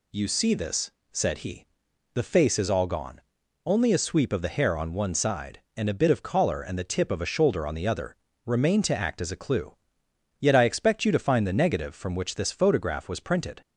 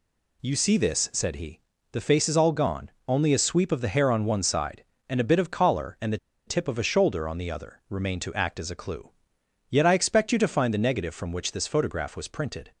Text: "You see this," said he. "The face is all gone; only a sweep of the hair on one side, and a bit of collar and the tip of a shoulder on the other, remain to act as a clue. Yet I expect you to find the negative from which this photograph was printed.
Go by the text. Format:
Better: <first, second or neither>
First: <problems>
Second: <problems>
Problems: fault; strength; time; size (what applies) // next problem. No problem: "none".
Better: first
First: none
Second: pauses between "the" and "tip"; slight; at 6.1 s; 0.29 s long